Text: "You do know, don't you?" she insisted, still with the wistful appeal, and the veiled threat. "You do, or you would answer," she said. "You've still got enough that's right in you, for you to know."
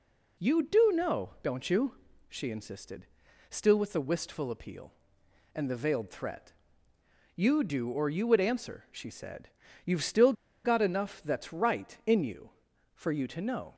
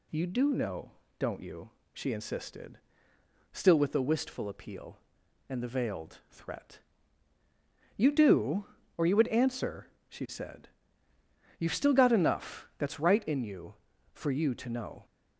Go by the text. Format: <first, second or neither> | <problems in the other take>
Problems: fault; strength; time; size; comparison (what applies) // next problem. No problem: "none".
second | pauses between "still" and "got"; slight; at 10.3 s; 0.31 s long